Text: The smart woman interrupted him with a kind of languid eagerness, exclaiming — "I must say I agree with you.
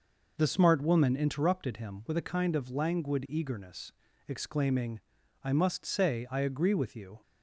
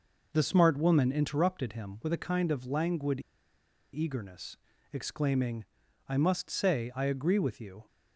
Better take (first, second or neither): first